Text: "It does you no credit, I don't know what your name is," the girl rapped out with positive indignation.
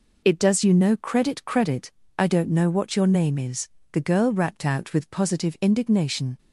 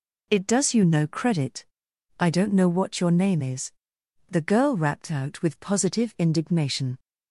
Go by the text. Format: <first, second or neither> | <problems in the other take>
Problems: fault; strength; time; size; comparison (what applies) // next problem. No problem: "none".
second | says "credit" twice; at 1.4 s